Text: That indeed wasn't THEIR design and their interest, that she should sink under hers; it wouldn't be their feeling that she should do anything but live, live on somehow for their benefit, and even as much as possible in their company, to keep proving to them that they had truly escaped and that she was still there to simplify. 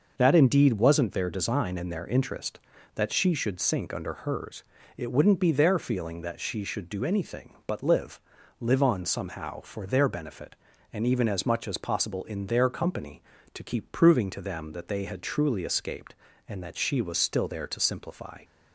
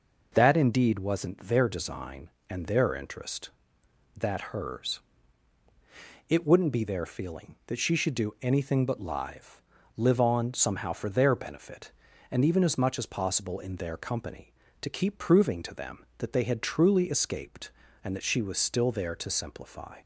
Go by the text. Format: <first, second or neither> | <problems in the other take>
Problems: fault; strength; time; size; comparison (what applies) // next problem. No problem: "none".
first | skips "she should sink under"; at 4.4 s